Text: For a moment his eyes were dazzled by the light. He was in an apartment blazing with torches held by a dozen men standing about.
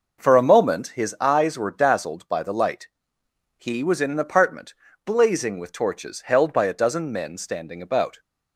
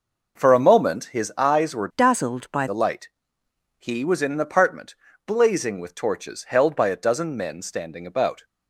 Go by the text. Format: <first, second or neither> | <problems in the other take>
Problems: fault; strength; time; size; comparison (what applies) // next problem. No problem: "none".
first | changes voice from "dazzled" to "by"; from 1.9 to 2.6 s; 0.7 s long // pauses between "apartment" and "blazing"; slight; at 4.9 s; 0.32 s long; slight in the first